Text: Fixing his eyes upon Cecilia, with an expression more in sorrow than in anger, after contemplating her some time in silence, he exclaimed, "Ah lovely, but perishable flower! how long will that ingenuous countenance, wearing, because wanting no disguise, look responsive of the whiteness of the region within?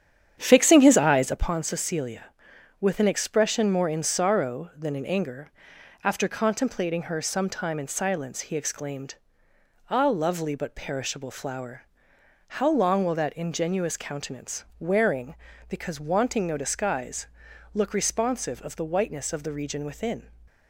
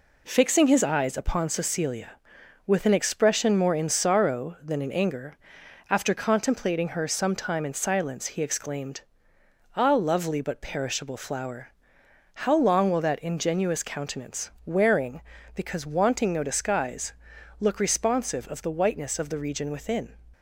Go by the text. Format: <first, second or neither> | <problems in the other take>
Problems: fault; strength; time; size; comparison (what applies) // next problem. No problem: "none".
second | starts louder than the rest; strong; until 1.5 s; 9 dB